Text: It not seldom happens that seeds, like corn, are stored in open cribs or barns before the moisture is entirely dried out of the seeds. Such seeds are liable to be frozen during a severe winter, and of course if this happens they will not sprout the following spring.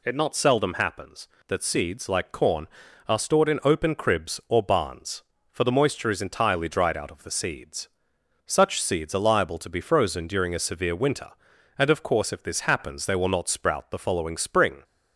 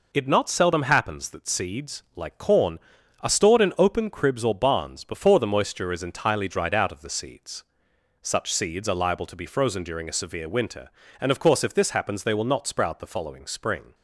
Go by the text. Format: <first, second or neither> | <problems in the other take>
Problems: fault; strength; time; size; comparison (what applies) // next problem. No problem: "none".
second | says "for" for "before"; at 5.5 s